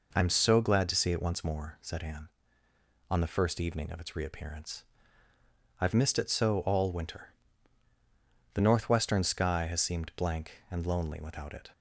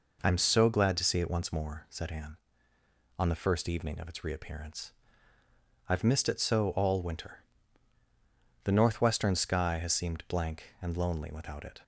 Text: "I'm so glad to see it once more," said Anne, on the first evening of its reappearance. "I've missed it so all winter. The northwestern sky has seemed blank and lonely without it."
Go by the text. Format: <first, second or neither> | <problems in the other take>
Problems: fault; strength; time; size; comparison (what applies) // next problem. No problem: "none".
neither | none